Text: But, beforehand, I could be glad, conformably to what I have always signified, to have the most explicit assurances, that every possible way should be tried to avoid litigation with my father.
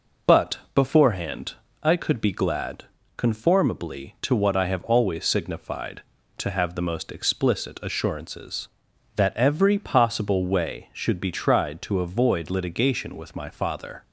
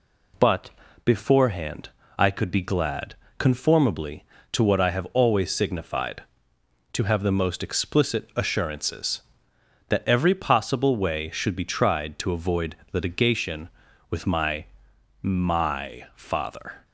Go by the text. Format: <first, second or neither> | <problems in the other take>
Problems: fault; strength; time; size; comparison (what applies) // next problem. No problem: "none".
first | pauses between "avoid" and "litigation"; slight; at 12.7 s; 0.18 s long // says "my" twice; at 15.2 s